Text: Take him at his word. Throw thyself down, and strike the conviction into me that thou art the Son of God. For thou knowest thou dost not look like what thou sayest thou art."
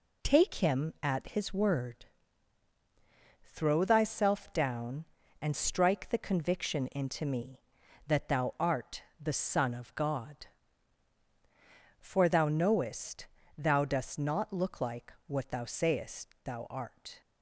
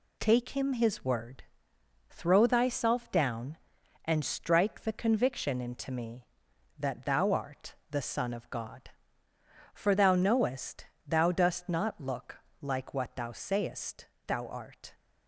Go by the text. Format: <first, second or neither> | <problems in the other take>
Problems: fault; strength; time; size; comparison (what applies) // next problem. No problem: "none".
first | skips "at"; at 0.7 s // pauses between "art" and "the"; slight; at 7.7 s; 0.16 s long; slight in the first // pauses between "knowest" and "thou"; slight; at 10.8 s; 0.20 s long; slight in the first // pauses between "look" and "like"; slight; at 12.3 s; 0.24 s long // pauses between "sayest" and "thou"; slight; at 14.0 s; 0.20 s long; slight in the first